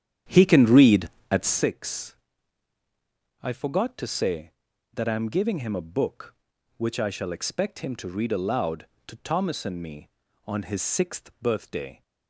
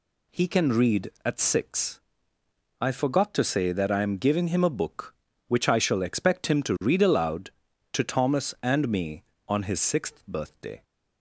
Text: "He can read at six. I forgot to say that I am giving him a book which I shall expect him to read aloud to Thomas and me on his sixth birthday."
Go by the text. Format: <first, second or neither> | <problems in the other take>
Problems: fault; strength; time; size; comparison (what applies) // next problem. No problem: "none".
second | starts louder than the rest; strong; until 1.6 s; 9.5 dB